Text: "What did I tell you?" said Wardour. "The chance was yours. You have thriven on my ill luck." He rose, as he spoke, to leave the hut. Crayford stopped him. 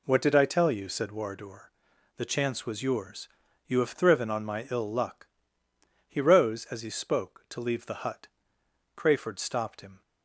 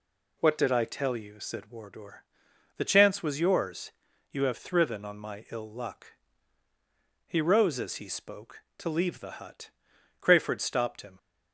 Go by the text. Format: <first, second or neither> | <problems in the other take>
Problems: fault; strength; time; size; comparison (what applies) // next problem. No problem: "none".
neither | none